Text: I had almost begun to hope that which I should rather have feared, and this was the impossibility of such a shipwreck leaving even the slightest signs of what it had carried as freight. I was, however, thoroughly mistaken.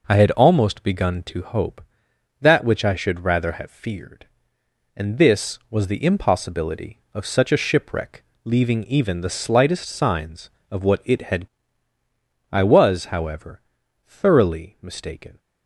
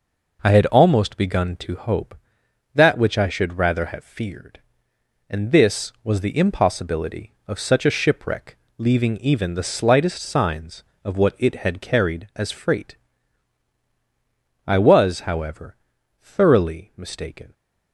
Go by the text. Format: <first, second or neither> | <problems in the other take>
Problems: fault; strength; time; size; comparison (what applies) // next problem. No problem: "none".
second | pauses between "shipwreck" and "leaving"; slight; at 8.2 s; 0.22 s long; slight in the second // skips "carried as freight"; at 11.9 s